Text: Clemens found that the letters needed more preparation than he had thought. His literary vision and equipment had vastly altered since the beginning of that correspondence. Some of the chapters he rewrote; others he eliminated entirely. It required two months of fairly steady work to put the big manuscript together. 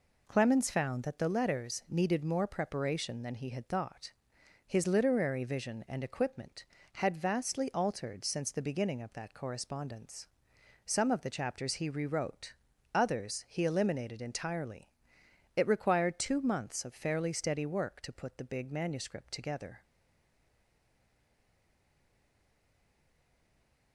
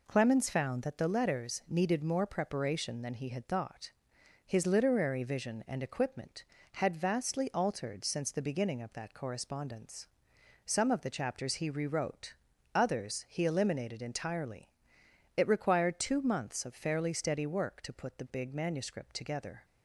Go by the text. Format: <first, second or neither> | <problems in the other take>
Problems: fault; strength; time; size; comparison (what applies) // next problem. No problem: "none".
second | stays silent after the last word; strong; from 19.8 s on; 4.1 s long